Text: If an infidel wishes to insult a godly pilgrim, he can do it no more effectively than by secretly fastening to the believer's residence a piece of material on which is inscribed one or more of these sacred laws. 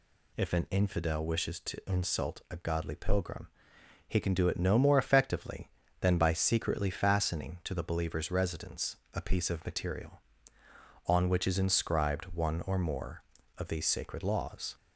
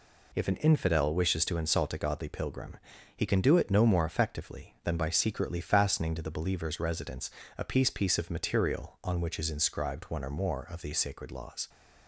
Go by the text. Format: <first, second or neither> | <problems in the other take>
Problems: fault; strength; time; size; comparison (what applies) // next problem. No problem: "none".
first | pauses between "residence" and "a"; slight; at 7.2 s; 0.30 s long; slight in the first // says "piece" twice; at 7.9 s